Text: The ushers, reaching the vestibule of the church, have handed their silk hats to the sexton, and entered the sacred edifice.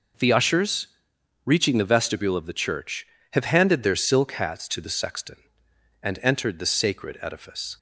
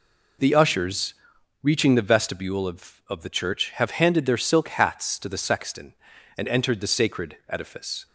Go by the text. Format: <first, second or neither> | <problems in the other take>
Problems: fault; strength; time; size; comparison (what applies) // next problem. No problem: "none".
first | says "of" twice; at 3.0 s